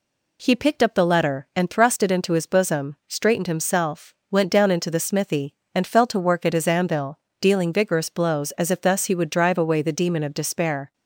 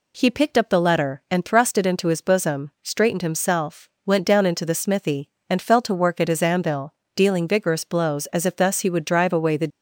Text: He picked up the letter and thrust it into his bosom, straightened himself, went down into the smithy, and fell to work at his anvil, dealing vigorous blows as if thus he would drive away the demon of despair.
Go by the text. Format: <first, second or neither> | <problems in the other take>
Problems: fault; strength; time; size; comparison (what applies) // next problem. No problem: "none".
first | stops before "demon of despair"; at 9.6 s